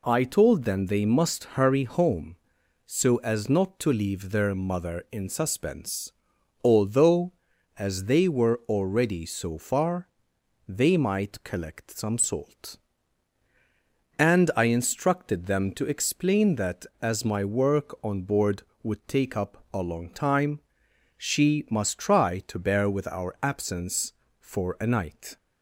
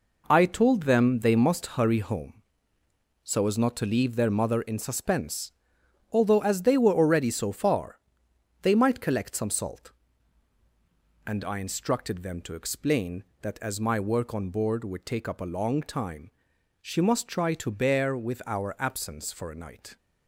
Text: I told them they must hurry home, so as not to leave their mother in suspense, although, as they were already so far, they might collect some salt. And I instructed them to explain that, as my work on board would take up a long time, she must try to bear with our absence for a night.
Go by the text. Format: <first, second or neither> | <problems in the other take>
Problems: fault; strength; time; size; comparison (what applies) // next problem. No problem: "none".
first | gets quieter; strong; throughout; 7.5 dB